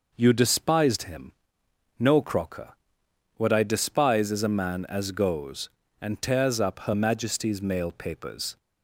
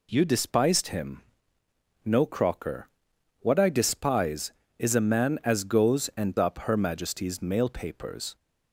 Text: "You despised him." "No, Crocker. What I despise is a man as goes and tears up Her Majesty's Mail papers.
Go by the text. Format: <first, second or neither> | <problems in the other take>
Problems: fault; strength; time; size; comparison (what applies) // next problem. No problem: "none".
first | skips "tears"; at 6.3 s